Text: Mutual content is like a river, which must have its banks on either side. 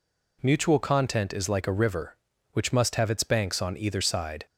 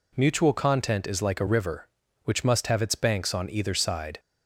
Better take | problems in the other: neither | none

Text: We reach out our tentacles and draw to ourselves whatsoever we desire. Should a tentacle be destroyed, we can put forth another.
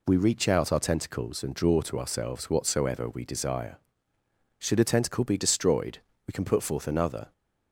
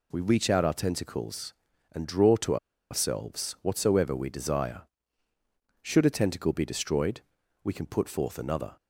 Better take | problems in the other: first | pauses between "to" and "ourselves"; slight; at 2.5 s; 0.34 s long

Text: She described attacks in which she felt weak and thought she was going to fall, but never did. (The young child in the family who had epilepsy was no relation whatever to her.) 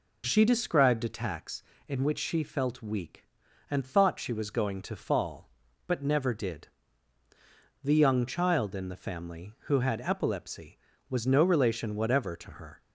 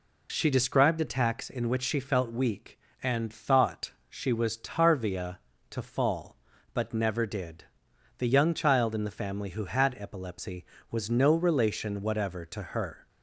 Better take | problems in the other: first | pauses between "thought" and "she"; slight; at 3.9 s; 0.16 s long // says "tarvia" for "going"; at 4.5 s

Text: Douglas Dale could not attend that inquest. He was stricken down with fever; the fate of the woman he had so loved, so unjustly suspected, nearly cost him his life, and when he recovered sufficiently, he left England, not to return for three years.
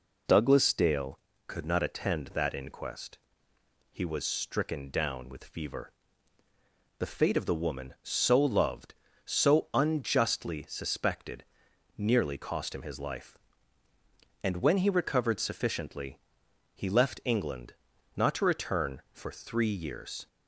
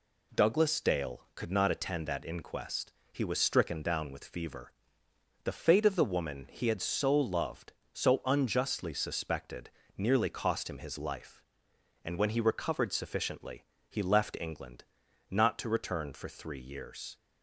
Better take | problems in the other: second | skips "he had"; at 7.9 s

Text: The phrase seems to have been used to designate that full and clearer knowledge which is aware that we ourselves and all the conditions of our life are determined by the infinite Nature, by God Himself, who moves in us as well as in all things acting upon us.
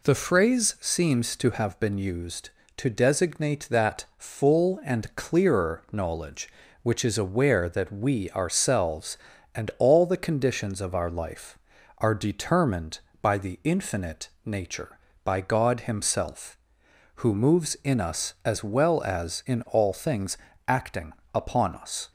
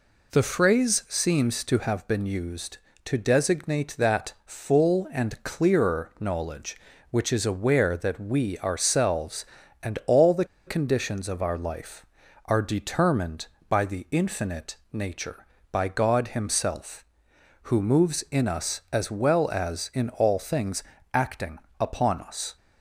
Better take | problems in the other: first | pauses between "the" and "conditions"; slight; at 10.4 s; 0.21 s long // pauses between "infinite" and "Nature"; slight; at 14.7 s; 0.18 s long; slight in the first // pauses between "things" and "acting"; slight; at 20.8 s; 0.32 s long; slight in the first // pauses between "acting" and "upon"; slight; at 21.6 s; 0.18 s long; slight in the first

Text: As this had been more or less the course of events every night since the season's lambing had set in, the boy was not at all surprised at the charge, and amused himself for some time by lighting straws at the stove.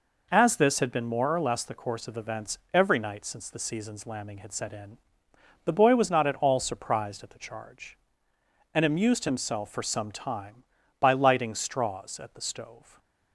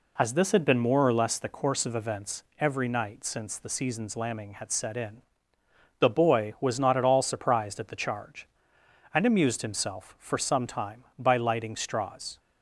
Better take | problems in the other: first | pauses between "events" and "every"; slight; at 2.4 s; 0.16 s long; slight in the first // stops before "at the stove"; at 12.3 s

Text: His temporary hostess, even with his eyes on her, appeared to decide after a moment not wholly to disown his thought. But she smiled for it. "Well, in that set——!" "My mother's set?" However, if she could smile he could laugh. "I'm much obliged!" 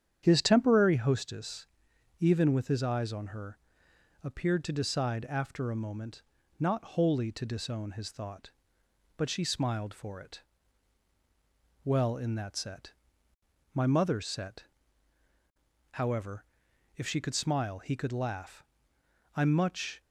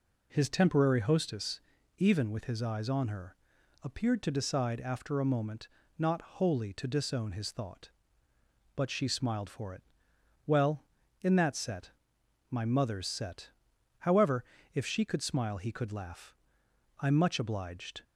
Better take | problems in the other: second | starts louder than the rest; strong; until 1.2 s; 9 dB // pauses between "moment" and "not"; slight; at 6.2 s; 0.36 s long; slight in the second // stops before "obliged"; at 20.0 s

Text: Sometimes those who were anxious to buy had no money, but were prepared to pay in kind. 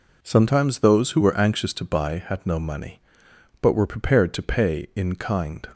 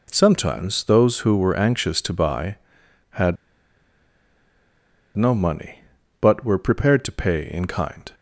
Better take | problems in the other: first | pauses between "had" and "no"; strong; at 3.3 s; 1.8 s long

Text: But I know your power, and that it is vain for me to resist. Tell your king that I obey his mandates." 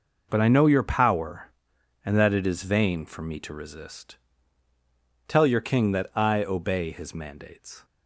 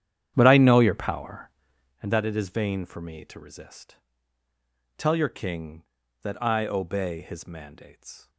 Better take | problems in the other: first | starts louder than the rest; strong; until 2.0 s; 10 dB

